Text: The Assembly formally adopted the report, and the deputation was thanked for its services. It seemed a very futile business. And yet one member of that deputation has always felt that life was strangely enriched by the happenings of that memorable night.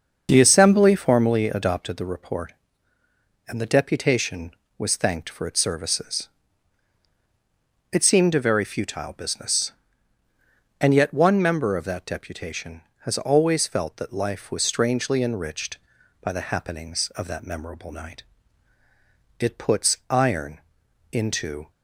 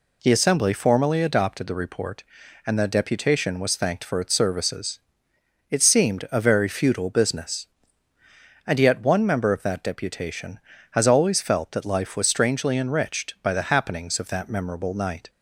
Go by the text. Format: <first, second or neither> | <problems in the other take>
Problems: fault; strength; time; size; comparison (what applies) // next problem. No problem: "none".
second | starts louder than the rest; until 1.3 s; 6.5 dB // goes on to say "It puts iron into"; strong; from 19.3 s on; 2.3 s long